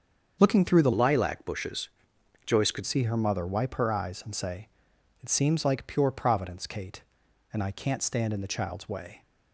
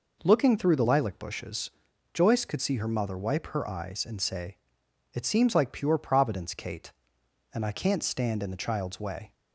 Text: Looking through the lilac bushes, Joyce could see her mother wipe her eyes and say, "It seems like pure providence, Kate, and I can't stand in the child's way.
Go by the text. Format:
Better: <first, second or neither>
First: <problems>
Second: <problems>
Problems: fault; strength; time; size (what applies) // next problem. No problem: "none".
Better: second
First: starts louder than the rest; until 1.4 s; 7 dB // changes voice from "lilac" to "could"; from 0.9 to 2.8 s; 1.9 s long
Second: none